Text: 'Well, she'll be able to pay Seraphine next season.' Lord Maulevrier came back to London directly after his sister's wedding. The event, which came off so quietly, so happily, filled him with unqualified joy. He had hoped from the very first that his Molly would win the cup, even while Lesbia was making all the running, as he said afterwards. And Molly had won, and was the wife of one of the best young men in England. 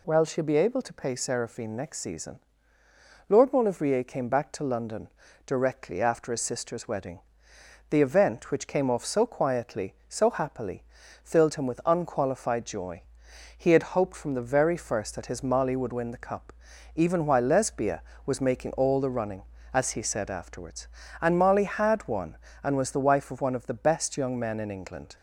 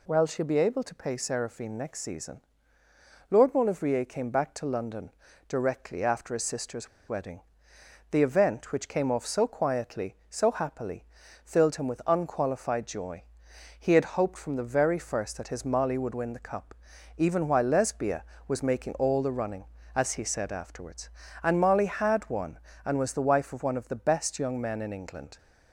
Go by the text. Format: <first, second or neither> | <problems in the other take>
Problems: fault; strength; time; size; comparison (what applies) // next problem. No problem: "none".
first | pauses between "London" and "directly"; at 5.1 s; 0.38 s long; also in the first // pauses between "sister's" and "wedding"; slight; at 6.8 s; 0.19 s long